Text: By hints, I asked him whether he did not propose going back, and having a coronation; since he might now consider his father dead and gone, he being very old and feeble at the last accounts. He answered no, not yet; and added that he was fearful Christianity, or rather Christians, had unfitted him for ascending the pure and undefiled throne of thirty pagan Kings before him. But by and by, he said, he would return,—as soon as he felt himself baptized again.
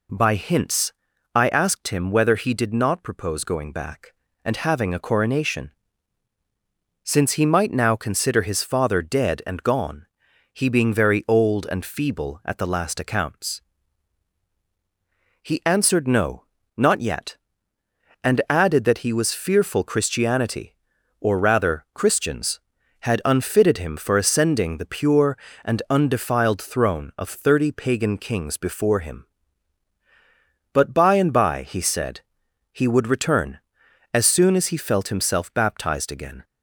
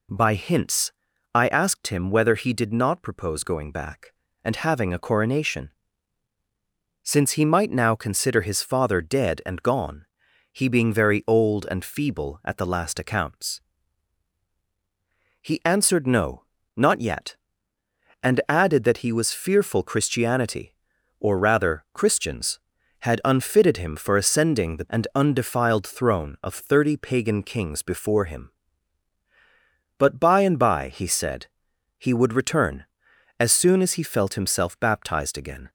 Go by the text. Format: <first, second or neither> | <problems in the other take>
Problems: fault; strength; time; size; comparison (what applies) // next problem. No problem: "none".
first | skips "pure"; at 24.8 s